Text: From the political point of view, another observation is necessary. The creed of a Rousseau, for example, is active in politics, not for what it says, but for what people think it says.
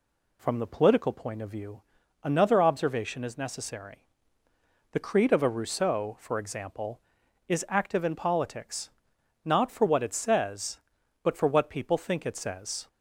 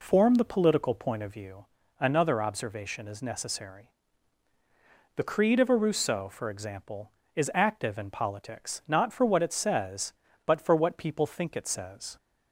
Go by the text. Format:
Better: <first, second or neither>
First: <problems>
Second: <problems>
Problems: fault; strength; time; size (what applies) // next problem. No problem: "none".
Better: first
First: none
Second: says "Form" for "From"; at 0.0 s